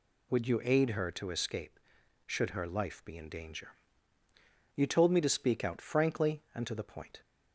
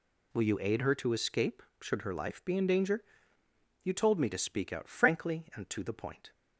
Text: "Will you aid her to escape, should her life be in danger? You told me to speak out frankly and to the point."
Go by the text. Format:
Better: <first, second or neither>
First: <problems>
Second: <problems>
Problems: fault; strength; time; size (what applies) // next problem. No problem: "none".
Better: second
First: says "Would" for "Will"; at 0.3 s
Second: none